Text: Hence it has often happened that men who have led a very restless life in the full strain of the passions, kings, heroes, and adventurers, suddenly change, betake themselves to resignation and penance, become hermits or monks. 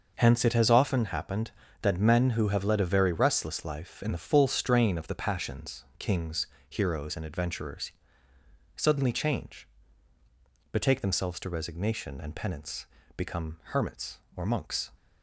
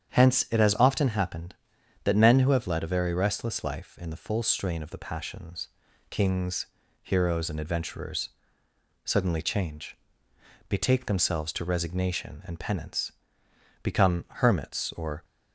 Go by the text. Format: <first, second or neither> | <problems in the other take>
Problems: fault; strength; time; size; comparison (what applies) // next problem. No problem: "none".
first | starts louder than the rest; strong; until 1.1 s; 8 dB; noticeable in the first // stops before "monks"; at 15.2 s